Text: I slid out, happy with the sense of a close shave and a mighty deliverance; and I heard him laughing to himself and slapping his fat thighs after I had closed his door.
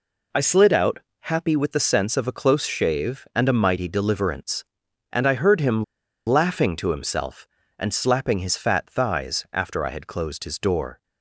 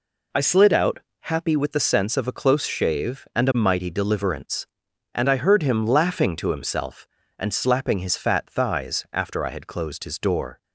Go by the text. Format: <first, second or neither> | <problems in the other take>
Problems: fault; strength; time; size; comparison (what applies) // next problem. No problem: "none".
second | pauses between "him" and "laughing"; at 5.8 s; 0.44 s long